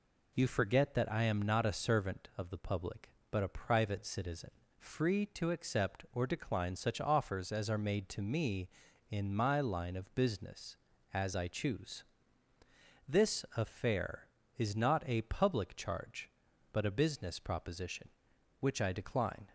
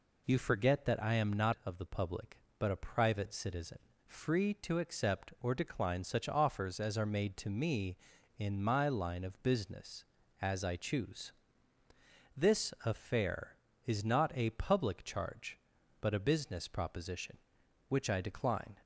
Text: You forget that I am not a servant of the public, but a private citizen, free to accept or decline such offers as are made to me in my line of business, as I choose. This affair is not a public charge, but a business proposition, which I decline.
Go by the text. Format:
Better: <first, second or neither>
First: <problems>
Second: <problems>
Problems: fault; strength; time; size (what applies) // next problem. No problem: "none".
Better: first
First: none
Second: skips "a servant"; at 1.5 s